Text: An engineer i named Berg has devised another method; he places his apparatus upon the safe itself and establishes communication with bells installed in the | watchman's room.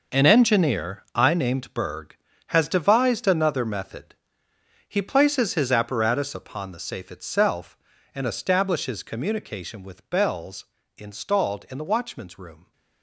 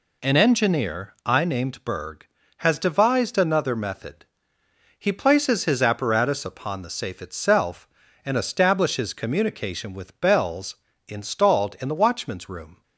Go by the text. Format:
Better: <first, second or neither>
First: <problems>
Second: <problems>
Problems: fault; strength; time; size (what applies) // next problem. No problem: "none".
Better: second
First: gets quieter; strong; throughout; 12 dB // pauses between "bells" and "installed"; slight; at 10.6 s; 0.34 s long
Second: pauses between "bells" and "installed"; slight; at 10.7 s; 0.34 s long